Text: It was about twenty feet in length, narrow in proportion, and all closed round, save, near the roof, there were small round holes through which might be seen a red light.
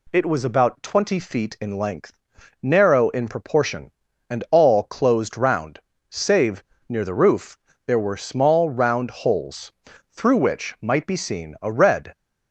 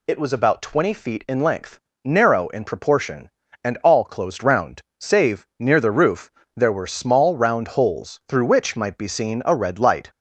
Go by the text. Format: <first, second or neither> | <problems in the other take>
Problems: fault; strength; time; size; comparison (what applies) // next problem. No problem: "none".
second | pauses between "holes" and "through"; at 9.6 s; 0.40 s long // stops before "light"; at 12.1 s